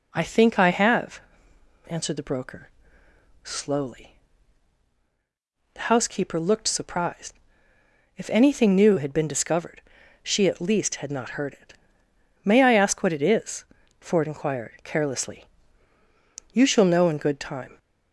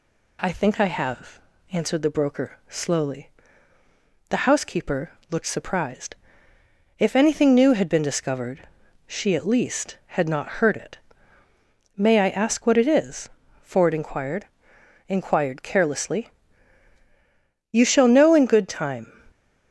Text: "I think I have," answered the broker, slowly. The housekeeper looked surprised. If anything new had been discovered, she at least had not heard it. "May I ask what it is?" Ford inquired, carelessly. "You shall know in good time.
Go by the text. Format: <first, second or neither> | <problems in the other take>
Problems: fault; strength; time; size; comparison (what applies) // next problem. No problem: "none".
first | pauses between "housekeeper" and "looked"; slight; at 5.1 s; 0.18 s long // says "inquired" twice; at 15.0 s